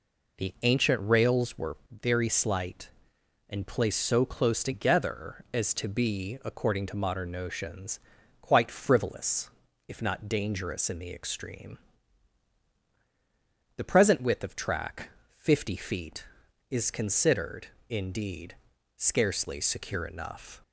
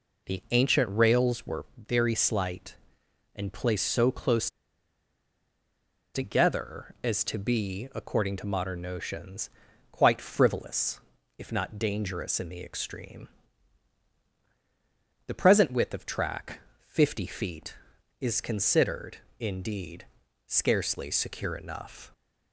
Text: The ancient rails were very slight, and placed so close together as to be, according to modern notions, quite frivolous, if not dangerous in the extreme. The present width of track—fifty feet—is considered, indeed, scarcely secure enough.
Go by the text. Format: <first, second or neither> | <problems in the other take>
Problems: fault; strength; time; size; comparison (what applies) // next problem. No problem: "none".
first | pauses between "close" and "together"; strong; at 4.4 s; 1.6 s long